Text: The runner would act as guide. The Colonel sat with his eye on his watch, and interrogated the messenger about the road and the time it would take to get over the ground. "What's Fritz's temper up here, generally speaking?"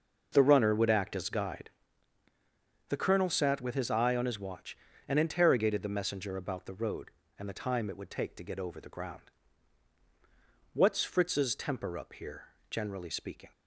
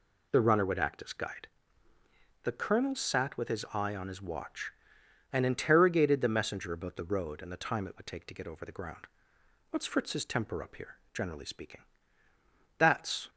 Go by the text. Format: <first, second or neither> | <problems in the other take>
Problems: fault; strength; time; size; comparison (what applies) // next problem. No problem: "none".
first | goes on to say "That's"; from 12.7 s on; 0.52 s long